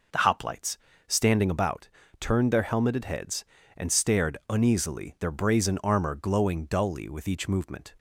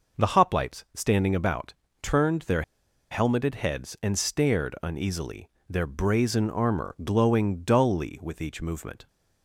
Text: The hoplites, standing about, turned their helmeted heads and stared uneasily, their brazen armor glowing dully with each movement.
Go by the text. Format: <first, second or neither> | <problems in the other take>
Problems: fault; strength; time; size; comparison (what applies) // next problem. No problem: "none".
first | pauses between "their" and "helmeted"; noticeable; at 2.6 s; 0.48 s long